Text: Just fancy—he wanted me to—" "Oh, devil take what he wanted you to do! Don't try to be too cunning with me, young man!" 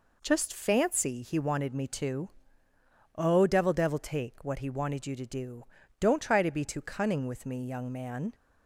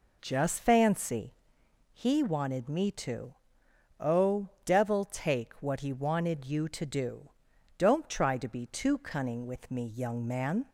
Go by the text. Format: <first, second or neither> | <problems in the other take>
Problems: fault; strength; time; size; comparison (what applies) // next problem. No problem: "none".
second | says "devil" twice; at 3.7 s